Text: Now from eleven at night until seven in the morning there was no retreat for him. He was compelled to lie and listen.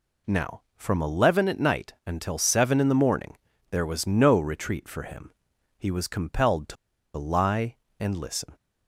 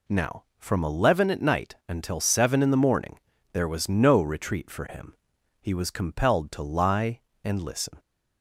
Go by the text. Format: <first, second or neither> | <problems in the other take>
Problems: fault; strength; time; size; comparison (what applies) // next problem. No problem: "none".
second | pauses between "morning" and "there"; slight; at 3.3 s; 0.34 s long; slight in the second // pauses between "to" and "lie"; at 6.7 s; 0.41 s long